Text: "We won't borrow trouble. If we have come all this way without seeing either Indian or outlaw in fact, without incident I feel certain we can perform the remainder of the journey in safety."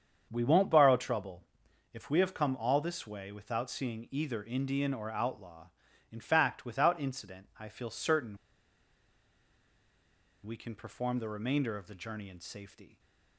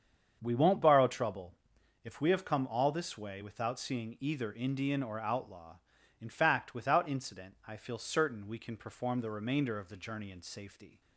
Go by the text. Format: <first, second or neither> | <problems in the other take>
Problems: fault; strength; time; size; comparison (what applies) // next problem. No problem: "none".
second | starts louder than the rest; strong; until 1.3 s; 7.5 dB; strong in the second // pauses between "certain" and "we"; strong; at 8.3 s; 2.0 s long // stays silent after the last word; slight; from 12.8 s on; 0.5 s long